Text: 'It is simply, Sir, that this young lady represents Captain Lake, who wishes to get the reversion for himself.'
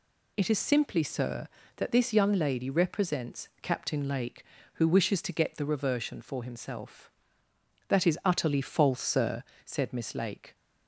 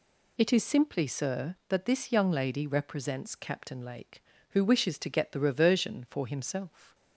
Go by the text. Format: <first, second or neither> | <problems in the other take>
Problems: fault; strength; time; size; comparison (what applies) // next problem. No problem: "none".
second | goes on to say "That is utterly false Sir said Miss Lake"; strong; from 7.8 s on; 2.6 s long